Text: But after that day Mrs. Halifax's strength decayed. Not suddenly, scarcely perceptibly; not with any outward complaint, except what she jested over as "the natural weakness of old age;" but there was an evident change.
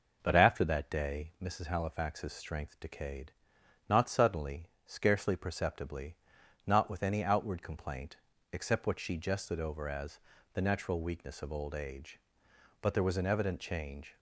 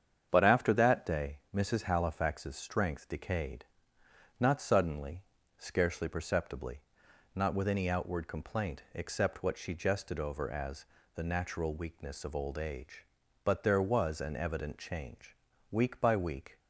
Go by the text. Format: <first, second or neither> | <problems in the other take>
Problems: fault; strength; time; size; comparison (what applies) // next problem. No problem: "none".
first | starts louder than the rest; strong; until 1.3 s; 8 dB // pauses between "as" and "the"; slight; at 10.8 s; 0.30 s long; slight in the first // goes on to say "Week by week"; noticeable; from 15.6 s on; 0.90 s long